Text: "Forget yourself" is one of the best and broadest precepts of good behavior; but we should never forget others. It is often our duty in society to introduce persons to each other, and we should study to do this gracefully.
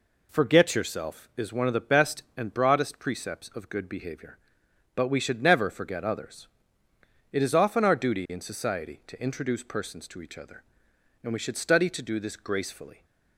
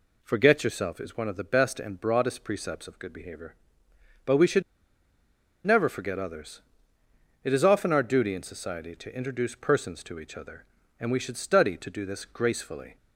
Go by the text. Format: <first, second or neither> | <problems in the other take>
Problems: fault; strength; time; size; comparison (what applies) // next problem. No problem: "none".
first | pauses between "should" and "never"; at 4.6 s; 1.0 s long